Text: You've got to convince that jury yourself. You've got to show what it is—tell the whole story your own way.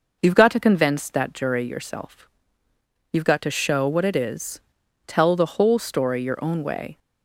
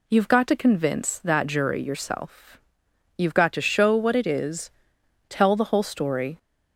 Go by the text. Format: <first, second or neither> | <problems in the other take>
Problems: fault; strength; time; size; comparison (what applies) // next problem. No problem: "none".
first | stops before "your own way"; at 6.3 s